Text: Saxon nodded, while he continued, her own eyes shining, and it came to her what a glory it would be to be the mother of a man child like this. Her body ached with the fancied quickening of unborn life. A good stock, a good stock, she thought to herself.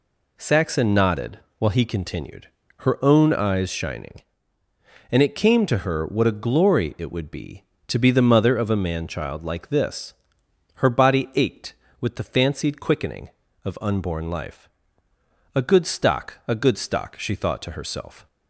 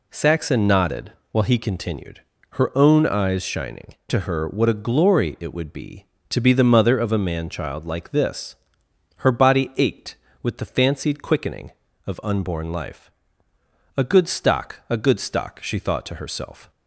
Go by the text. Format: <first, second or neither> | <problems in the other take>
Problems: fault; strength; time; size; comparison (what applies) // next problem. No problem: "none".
first | skips "and it came"; at 4.0 s